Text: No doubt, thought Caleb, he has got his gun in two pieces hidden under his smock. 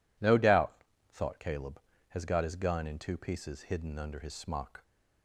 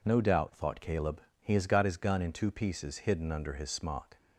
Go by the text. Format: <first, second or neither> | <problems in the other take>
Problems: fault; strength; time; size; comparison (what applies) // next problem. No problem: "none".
second | skips "he"; at 1.9 s